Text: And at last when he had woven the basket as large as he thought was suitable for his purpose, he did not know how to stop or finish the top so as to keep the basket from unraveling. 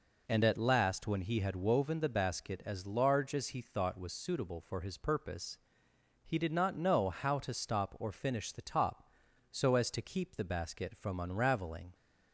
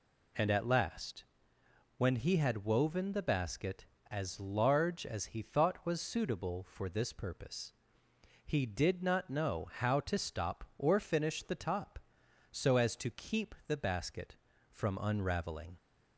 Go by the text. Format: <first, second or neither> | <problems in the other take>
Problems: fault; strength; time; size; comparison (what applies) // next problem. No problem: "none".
first | pauses between "last" and "when"; noticeable; at 1.2 s; 0.72 s long // says "this" for "his"; at 6.8 s